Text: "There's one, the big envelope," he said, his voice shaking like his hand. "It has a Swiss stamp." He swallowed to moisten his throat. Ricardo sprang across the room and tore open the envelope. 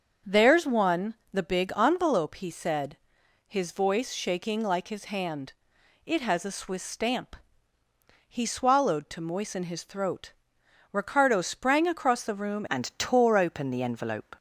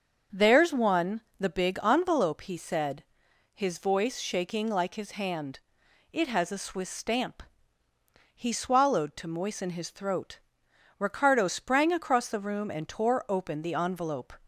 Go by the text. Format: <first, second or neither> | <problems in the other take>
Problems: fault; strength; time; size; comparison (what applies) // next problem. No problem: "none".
second | starts louder than the rest; until 1.4 s; 7 dB; also in the second // changes voice at "and"; from 12.7 s on; 1.6 s long